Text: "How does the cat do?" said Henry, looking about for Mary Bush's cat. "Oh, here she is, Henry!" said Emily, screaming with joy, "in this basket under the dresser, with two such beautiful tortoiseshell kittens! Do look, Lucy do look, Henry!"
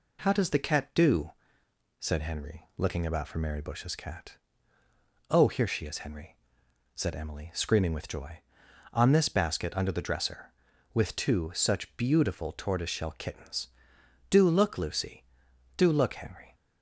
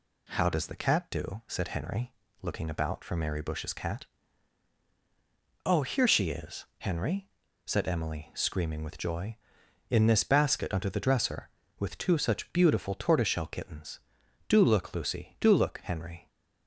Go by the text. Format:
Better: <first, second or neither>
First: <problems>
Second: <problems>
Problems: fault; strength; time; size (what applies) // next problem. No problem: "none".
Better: second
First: says "on" for "in"; at 8.9 s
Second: none